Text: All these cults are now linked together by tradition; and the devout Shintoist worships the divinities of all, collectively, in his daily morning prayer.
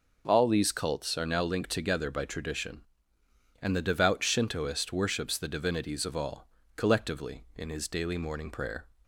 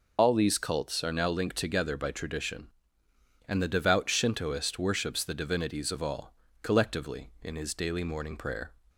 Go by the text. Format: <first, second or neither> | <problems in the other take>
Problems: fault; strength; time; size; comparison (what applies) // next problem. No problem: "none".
first | loses the start of "All"; at 0.1 s; 75 ms